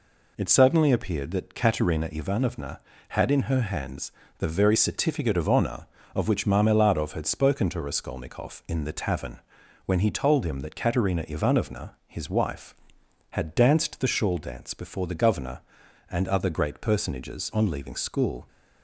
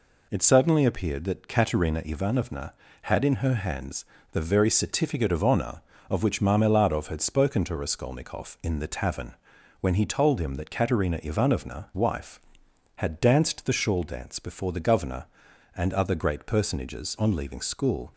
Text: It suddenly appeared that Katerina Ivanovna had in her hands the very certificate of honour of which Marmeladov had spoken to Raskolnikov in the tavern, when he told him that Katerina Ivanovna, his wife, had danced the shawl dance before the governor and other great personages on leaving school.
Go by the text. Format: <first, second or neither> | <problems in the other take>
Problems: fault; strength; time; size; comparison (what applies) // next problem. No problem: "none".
first | pauses between "hands" and "the"; slight; at 4.0 s; 0.28 s long; slight in the first // skips "his"; at 11.9 s